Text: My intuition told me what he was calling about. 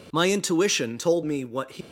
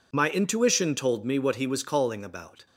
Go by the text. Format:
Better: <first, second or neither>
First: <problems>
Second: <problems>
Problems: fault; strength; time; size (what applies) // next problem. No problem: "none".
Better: second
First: stops before "was calling about"; at 1.8 s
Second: none